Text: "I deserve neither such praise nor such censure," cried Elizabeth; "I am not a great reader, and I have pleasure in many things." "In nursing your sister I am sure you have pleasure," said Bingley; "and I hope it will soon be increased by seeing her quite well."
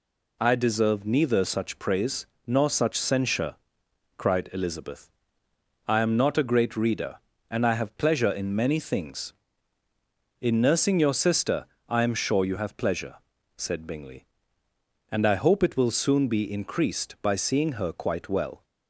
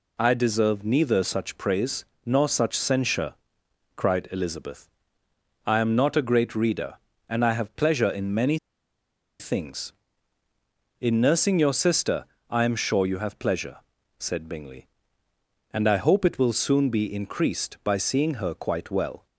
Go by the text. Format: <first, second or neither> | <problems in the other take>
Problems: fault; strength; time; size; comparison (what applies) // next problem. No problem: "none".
first | pauses between "praise" and "nor"; slight; at 2.0 s; 0.20 s long; slight in the first // pauses between "many" and "things"; noticeable; at 8.5 s; 0.82 s long // pauses between "sister" and "I"; slight; at 12.2 s; 0.24 s long; slight in the first